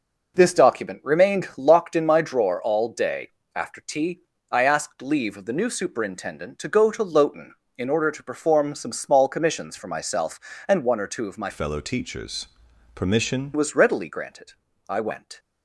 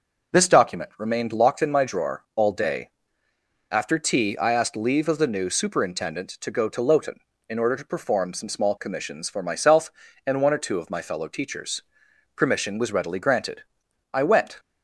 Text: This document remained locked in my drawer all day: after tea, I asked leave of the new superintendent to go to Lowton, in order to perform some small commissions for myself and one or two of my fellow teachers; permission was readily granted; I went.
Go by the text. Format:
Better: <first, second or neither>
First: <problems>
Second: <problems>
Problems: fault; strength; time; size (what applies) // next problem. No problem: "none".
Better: second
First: changes voice from "fellow" to "permission"; from 11.5 to 13.5 s; 2.0 s long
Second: none